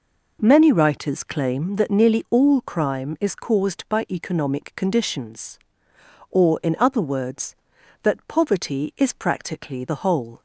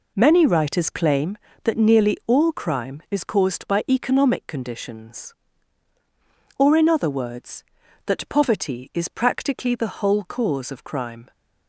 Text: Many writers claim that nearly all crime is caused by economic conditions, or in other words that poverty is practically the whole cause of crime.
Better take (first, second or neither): second